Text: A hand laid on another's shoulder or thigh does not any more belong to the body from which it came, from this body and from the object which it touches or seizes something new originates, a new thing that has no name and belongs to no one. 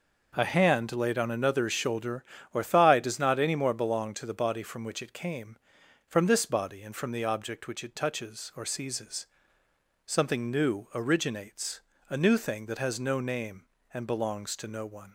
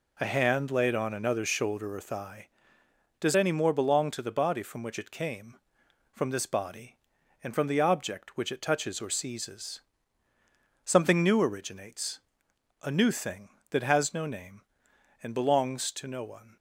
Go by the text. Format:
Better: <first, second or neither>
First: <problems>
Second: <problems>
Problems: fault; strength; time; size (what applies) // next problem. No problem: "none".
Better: first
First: pauses between "seizes" and "something"; noticeable; at 9.2 s; 0.80 s long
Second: skips "not"; at 3.3 s // pauses between "seizes" and "something"; at 9.8 s; 1.0 s long